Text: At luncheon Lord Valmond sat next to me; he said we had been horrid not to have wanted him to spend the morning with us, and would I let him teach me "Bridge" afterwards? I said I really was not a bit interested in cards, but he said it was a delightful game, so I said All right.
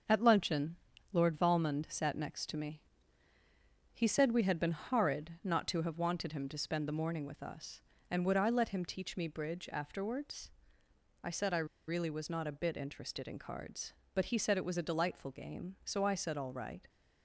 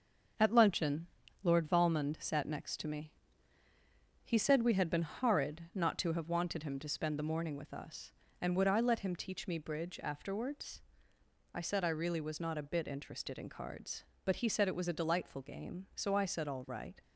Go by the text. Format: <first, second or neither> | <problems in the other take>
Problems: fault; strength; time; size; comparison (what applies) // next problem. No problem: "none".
second | starts louder than the rest; until 1.4 s; 6.5 dB; also in the second // pauses between "luncheon" and "Lord"; at 0.7 s; 0.38 s long; also in the second // pauses between "I" and "really"; slight; at 11.6 s; 0.22 s long